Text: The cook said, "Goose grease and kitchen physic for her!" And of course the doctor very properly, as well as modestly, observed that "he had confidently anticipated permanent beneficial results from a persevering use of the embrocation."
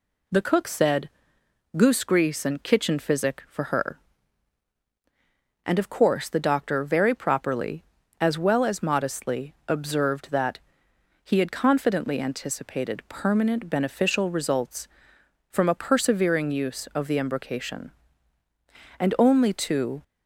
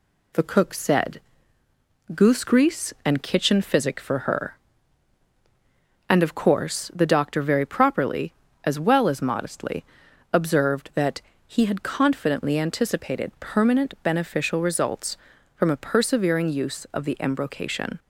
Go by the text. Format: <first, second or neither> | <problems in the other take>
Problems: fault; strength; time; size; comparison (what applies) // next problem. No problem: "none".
second | pauses between "that" and "he"; noticeable; at 10.5 s; 0.64 s long; slight in the second // goes on to say "And only to"; noticeable; from 18.9 s on; 1.0 s long